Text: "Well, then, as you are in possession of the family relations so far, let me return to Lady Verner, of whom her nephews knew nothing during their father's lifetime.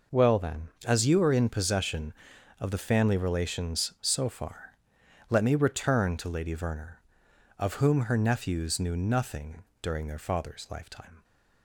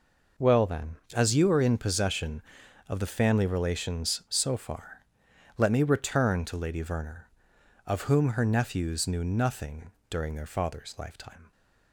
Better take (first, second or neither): neither